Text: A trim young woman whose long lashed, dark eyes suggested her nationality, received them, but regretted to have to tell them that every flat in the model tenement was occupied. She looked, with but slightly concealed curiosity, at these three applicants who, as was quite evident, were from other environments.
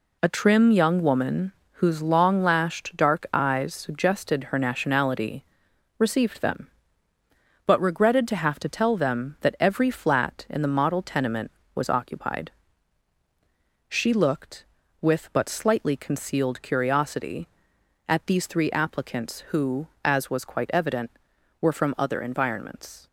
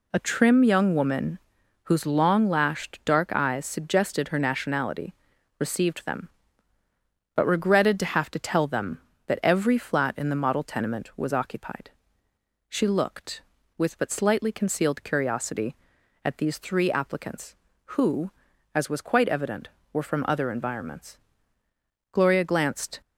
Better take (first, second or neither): first